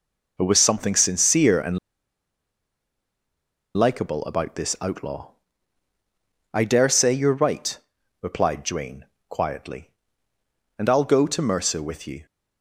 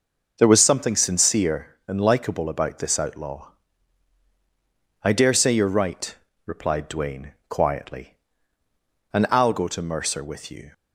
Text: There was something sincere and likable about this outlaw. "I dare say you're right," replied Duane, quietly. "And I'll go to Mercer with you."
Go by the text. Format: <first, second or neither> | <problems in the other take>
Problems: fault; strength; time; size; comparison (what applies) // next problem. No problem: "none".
second | pauses between "and" and "likable"; strong; at 1.7 s; 1.9 s long